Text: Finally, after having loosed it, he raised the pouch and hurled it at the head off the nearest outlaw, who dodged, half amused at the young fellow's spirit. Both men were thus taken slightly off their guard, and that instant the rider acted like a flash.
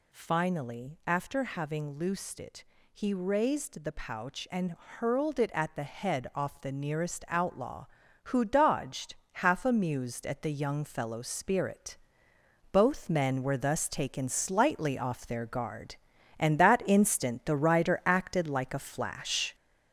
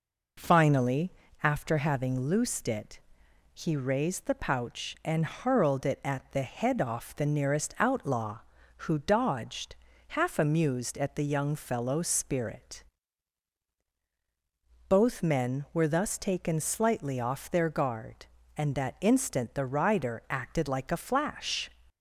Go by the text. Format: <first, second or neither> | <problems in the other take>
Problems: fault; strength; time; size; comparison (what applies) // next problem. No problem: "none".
second | gets louder; throughout; 6.5 dB